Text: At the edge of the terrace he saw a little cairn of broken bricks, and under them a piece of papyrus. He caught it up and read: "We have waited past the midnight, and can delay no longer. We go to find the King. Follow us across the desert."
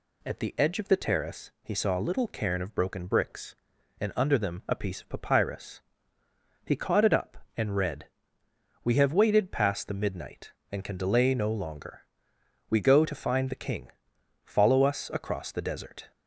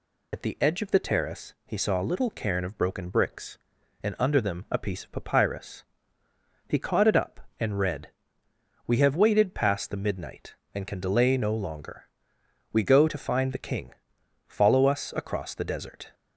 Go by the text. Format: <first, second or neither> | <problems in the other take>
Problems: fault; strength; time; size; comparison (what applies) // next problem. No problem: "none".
first | loses the start of "At"; at 0.3 s; 75 ms